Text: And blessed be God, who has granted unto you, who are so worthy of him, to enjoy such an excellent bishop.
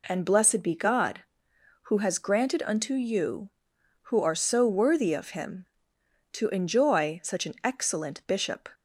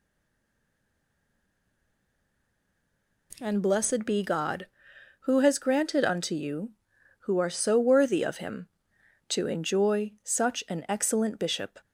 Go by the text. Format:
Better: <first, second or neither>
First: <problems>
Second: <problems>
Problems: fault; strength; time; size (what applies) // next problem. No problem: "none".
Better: first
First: none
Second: stays silent before the first word; strong; until 3.3 s; 3.3 s long